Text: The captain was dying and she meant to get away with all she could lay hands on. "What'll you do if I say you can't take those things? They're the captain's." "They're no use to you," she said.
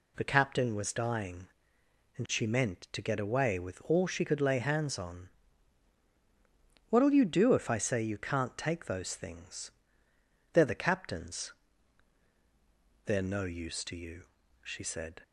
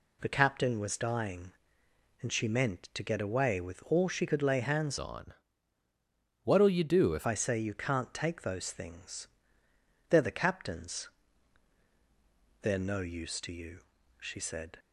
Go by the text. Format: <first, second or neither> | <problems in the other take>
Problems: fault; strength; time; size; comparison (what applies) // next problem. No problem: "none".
first | changes voice from "on" to "if"; from 4.9 to 7.2 s; 2.3 s long